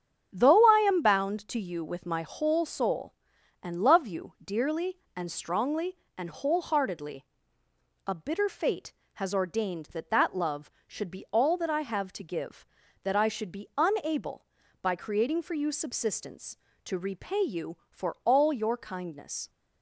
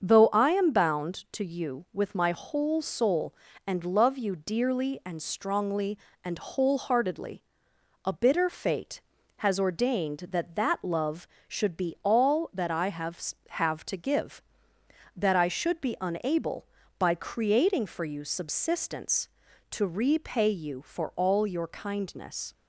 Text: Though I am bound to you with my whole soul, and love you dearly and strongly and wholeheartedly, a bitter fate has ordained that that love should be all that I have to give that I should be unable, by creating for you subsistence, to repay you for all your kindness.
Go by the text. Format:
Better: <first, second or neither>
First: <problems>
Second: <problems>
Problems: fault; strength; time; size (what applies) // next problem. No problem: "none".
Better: first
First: starts louder than the rest; strong; until 1.3 s; 8 dB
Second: starts louder than the rest; until 1.0 s; 7 dB // says "have" twice; at 13.4 s